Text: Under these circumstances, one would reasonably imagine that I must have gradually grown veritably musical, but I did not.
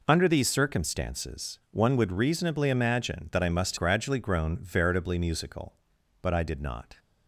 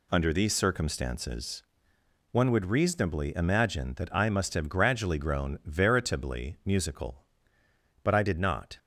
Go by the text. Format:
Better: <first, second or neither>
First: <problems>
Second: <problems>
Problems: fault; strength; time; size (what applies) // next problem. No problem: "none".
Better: second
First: skips "have"; at 3.7 s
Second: none